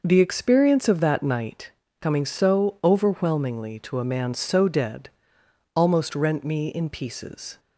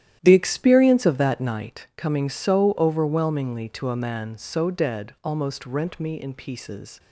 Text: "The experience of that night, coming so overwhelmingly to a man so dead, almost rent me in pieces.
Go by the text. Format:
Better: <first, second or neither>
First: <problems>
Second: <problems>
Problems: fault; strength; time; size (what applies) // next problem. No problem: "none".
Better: first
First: none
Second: starts louder than the rest; strong; until 1.9 s; 11.5 dB